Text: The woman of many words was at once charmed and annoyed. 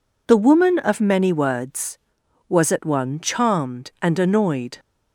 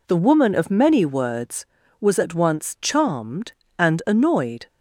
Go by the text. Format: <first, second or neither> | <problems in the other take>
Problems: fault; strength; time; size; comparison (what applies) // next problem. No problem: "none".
second | says "one" for "once"; at 2.8 s